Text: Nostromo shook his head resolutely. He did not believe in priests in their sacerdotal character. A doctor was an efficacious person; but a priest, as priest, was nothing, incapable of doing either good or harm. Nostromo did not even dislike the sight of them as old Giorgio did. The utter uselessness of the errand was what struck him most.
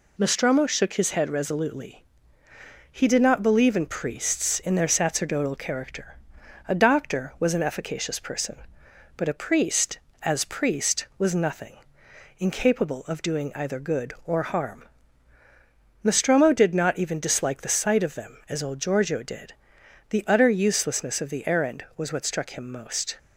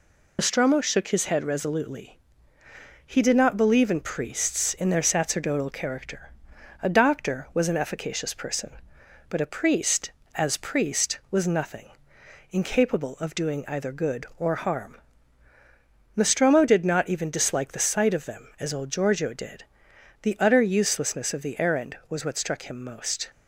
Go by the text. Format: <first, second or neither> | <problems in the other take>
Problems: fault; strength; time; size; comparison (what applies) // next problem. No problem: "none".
first | loses the start of "Nostromo"; at 0.3 s; 60 ms